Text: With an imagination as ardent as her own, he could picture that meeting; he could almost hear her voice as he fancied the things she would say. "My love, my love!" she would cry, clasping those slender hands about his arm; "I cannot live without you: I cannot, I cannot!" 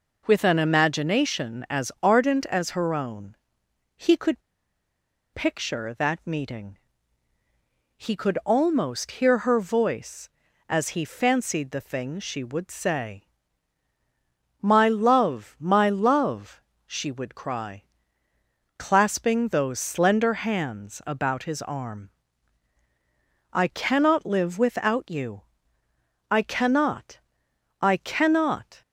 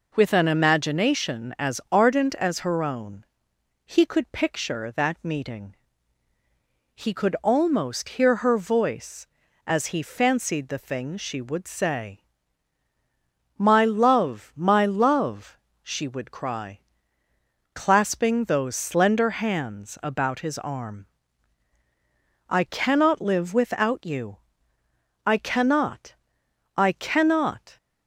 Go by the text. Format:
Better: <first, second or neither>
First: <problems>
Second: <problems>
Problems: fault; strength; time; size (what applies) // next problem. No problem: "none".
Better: second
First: pauses between "could" and "picture"; noticeable; at 4.4 s; 0.94 s long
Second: none